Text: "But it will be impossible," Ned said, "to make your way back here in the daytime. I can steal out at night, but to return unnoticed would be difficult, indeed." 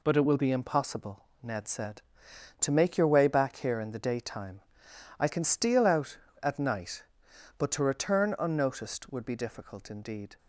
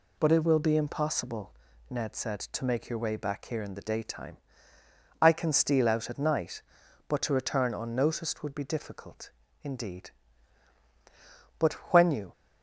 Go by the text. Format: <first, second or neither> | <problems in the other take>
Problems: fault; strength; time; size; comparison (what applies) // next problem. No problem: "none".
first | goes on to say "But when you"; noticeable; from 11.5 s on; 0.74 s long